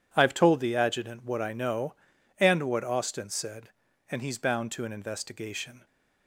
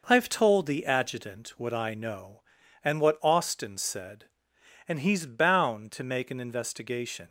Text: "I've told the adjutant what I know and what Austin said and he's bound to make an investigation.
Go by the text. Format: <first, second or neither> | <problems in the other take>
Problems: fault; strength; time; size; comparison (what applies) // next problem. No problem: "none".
second | skips "make"; at 4.8 s